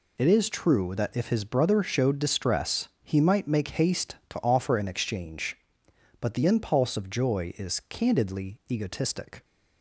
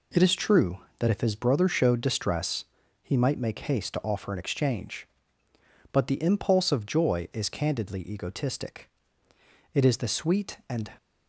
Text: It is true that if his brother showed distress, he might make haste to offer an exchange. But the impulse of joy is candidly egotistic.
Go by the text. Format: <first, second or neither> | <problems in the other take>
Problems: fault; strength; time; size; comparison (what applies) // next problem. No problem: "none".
first | goes on to say "It is the sweet and"; noticeable; from 9.7 s on; 1.1 s long